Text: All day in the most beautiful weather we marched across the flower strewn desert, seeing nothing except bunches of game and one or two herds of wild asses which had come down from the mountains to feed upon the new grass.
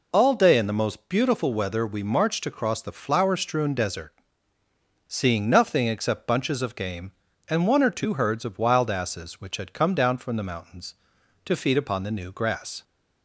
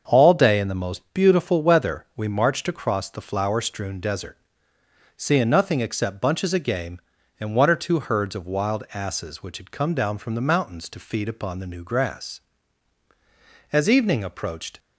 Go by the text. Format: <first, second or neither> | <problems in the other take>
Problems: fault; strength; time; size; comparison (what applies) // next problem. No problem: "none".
first | starts louder than the rest; until 1.2 s; 7 dB // goes on to say "As evening approached"; noticeable; from 13.7 s on; 1.0 s long